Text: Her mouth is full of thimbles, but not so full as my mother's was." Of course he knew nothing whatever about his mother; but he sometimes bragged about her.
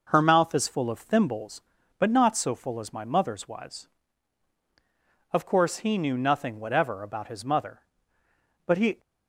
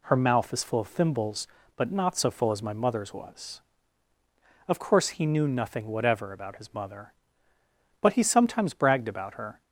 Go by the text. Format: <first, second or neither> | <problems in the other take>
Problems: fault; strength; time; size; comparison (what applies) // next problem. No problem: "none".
second | stops before "sometimes bragged about her"; at 8.9 s